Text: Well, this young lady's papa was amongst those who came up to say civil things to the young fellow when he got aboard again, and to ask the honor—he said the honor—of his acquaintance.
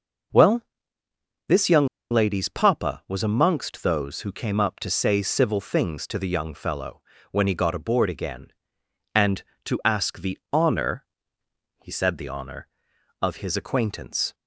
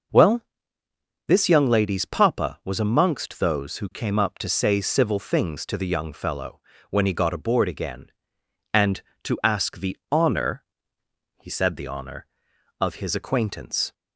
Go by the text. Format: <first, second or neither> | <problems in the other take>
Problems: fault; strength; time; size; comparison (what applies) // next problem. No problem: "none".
second | pauses between "young" and "lady's"; slight; at 1.8 s; 0.24 s long // pauses between "fellow" and "when"; slight; at 7.0 s; 0.30 s long; slight in the second